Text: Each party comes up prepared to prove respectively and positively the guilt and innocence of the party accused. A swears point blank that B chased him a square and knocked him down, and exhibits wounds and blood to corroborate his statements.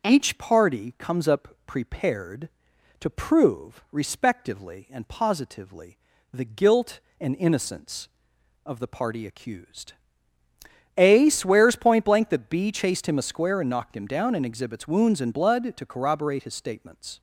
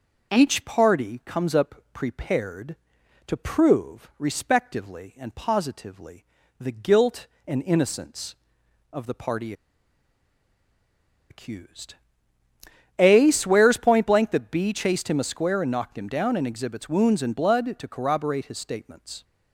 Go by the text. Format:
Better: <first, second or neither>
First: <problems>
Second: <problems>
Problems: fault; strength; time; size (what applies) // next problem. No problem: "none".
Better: first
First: pauses between "up" and "prepared"; slight; at 1.4 s; 0.18 s long // pauses between "positively" and "the"; slight; at 5.9 s; 0.34 s long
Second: pauses between "up" and "prepared"; slight; at 1.7 s; 0.18 s long // pauses between "positively" and "the"; slight; at 6.2 s; 0.34 s long // pauses between "party" and "accused"; strong; at 9.5 s; 1.7 s long